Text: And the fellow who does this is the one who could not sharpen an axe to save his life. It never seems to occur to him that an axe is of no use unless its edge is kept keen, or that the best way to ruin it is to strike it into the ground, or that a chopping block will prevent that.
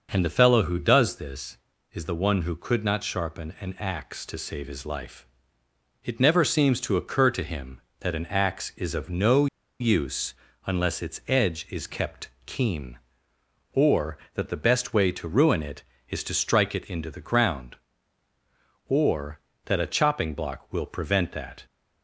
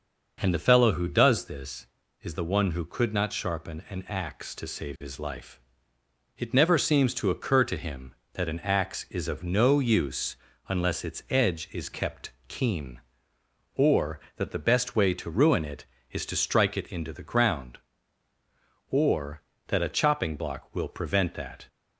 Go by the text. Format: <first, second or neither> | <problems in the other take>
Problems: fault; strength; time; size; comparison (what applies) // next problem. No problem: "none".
second | pauses between "no" and "use"; slight; at 9.4 s; 0.34 s long // pauses between "use" and "unless"; slight; at 10.3 s; 0.32 s long; slight in the second // pauses between "kept" and "keen"; slight; at 12.2 s; 0.16 s long; slight in the second